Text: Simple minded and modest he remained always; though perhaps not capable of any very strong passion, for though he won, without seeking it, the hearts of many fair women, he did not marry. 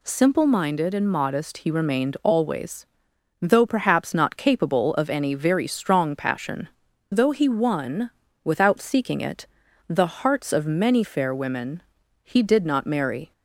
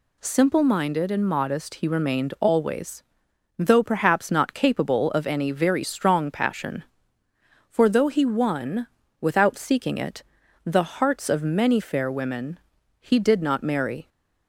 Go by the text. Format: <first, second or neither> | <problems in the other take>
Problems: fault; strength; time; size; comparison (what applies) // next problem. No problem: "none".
second | skips "for"; at 6.9 s